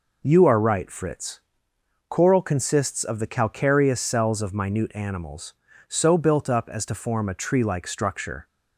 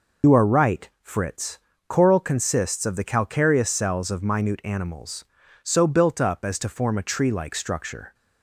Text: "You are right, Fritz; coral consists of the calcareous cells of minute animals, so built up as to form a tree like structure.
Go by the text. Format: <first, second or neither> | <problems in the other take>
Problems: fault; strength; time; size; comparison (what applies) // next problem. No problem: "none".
first | loses the start of "You"; at 0.2 s; 75 ms